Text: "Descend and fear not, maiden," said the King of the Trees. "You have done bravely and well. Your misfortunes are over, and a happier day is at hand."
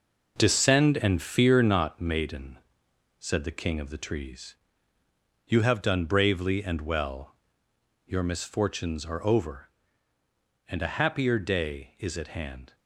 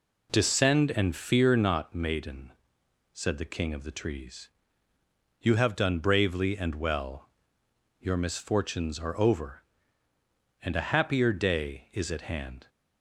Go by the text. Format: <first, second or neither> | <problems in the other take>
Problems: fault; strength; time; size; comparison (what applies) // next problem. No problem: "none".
second | gets quieter; strong; throughout; 8 dB